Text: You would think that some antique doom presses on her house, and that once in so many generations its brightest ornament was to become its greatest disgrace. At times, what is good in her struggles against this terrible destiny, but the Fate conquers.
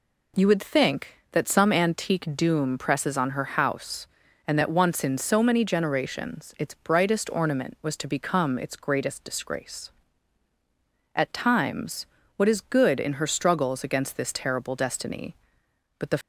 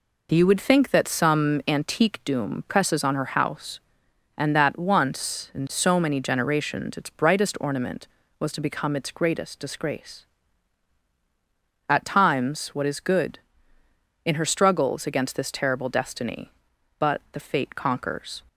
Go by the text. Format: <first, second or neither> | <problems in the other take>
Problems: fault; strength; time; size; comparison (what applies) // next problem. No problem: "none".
second | stops before "Fate conquers"; at 16.2 s